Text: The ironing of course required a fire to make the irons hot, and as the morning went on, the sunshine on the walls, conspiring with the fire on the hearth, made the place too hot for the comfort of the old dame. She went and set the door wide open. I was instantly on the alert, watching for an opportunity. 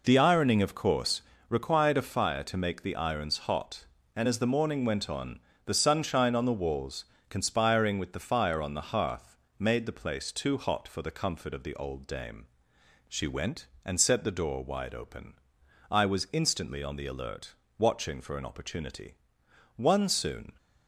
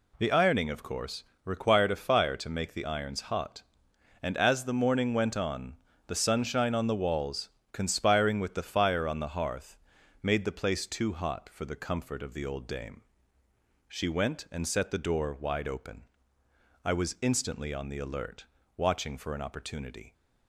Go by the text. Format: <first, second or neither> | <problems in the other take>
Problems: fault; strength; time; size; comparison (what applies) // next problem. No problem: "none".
second | pauses between "course" and "required"; slight; at 1.2 s; 0.28 s long; slight in the second // goes on to say "One soon"; noticeable; from 19.7 s on; 0.76 s long